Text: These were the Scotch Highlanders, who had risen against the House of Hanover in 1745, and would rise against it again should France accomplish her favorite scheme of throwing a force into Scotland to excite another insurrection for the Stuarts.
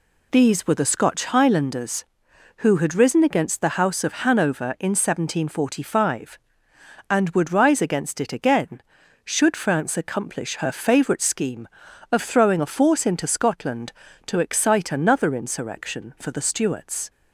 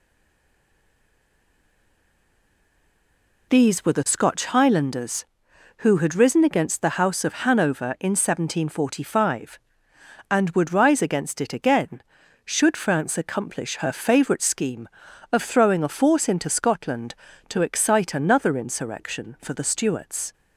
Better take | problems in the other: first | stays silent before the first word; strong; until 3.4 s; 3.4 s long

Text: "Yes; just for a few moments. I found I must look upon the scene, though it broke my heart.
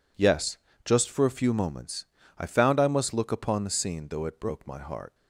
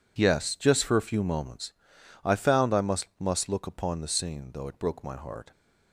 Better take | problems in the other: first | says "must" twice; at 3.1 s

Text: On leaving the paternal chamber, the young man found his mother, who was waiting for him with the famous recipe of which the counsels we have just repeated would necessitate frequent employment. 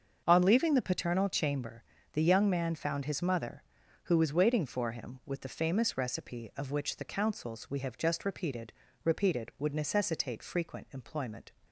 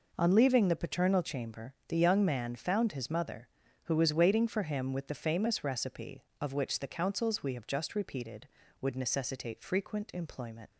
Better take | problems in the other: second | starts louder than the rest; until 1.2 s; 6.5 dB // says "repeated" twice; at 9.0 s

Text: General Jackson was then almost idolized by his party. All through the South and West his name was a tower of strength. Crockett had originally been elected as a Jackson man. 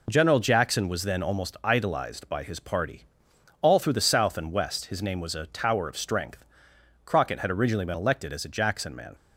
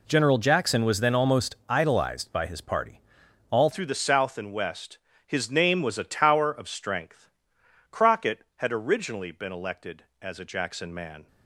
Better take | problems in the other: first | changes voice at "through"; from 3.7 s on; 7.5 s long // pauses between "West" and "his"; slight; at 4.9 s; 0.30 s long

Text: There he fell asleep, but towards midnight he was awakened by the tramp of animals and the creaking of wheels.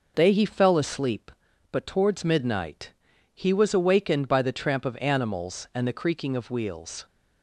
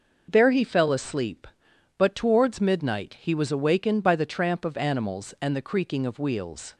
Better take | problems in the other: second | says "They" for "There"; at 0.1 s // pauses between "midnight" and "he"; at 2.9 s; 0.40 s long

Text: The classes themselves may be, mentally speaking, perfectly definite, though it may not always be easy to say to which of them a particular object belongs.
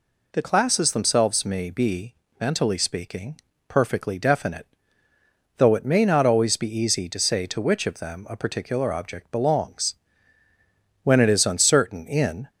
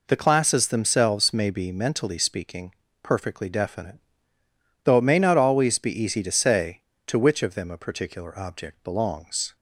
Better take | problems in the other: second | goes on to say "When it is uncertain in"; from 11.0 s on; 1.4 s long

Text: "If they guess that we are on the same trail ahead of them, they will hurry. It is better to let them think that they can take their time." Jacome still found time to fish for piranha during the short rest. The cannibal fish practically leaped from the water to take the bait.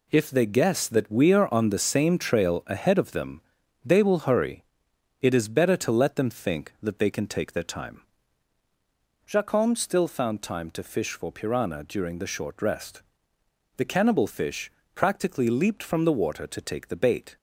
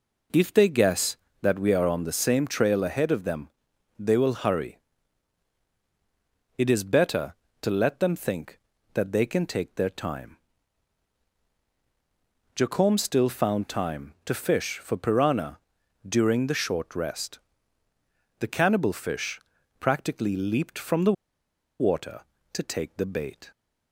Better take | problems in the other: first | pauses between "piranha" and "during"; noticeable; at 15.5 s; 0.50 s long // pauses between "fish" and "practically"; at 19.3 s; 0.40 s long; slight in the first // pauses between "the" and "water"; noticeable; at 21.1 s; 0.67 s long

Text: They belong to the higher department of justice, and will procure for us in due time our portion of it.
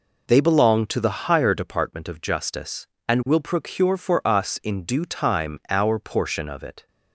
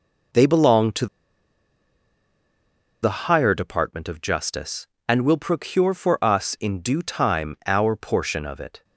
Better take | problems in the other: first | pauses between "to" and "the"; strong; at 1.0 s; 1.9 s long

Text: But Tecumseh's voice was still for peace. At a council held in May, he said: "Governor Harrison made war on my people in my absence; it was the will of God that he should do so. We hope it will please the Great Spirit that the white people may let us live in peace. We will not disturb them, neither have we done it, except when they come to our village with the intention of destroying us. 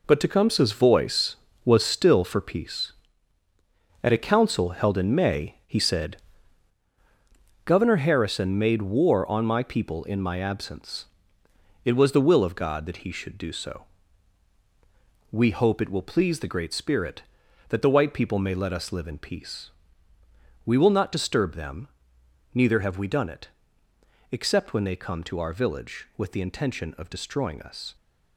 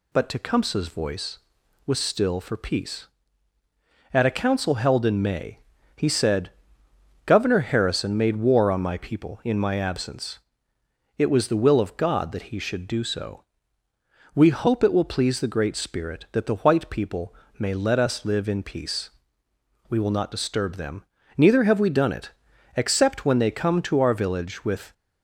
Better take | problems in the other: first | pauses between "people" and "may"; slight; at 17.3 s; 0.24 s long // stops before "the intention of destroying us"; at 24.9 s

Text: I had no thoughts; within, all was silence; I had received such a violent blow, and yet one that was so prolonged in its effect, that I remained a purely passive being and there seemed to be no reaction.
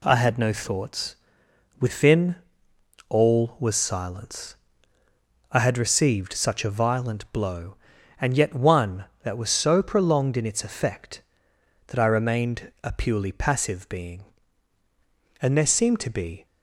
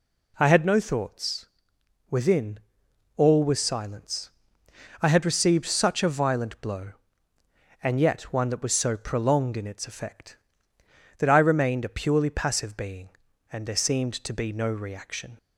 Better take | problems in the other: second | stops before "no reaction"; at 16.4 s

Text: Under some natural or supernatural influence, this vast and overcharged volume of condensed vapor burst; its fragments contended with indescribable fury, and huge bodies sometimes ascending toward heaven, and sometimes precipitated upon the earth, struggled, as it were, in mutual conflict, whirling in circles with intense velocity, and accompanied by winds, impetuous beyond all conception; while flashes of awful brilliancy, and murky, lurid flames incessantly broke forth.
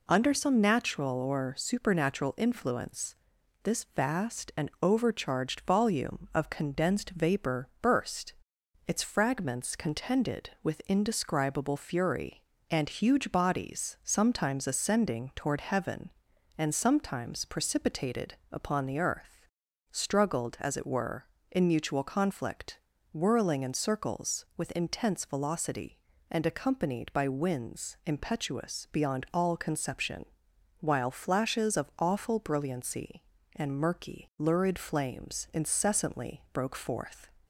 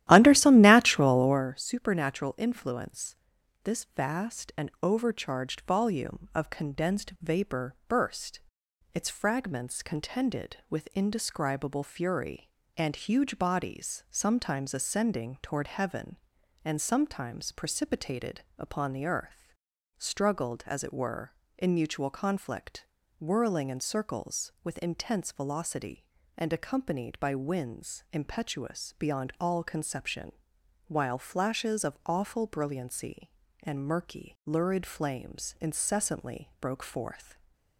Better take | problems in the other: first | starts louder than the rest; strong; until 1.5 s; 13.5 dB // pauses between "precipitated" and "upon"; slight; at 18.4 s; 0.16 s long; slight in the first

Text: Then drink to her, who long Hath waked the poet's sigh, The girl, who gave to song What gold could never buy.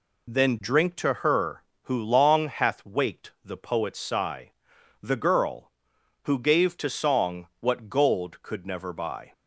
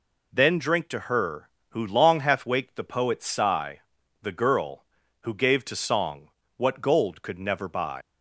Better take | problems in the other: first | pauses between "song" and "What"; slight; at 6.3 s; 0.26 s long // leaves "buy" unfinished; at 8.0 s; 100 ms

